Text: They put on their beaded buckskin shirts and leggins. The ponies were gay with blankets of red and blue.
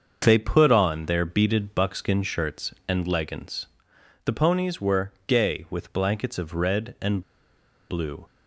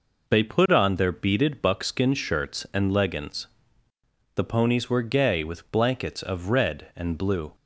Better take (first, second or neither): second